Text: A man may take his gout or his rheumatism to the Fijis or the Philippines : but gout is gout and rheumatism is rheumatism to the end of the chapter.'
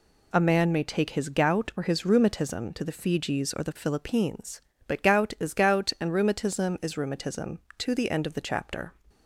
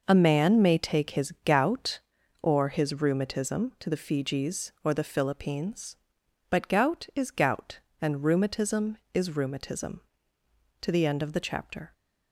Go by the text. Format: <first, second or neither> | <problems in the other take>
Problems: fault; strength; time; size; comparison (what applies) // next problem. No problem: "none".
neither | none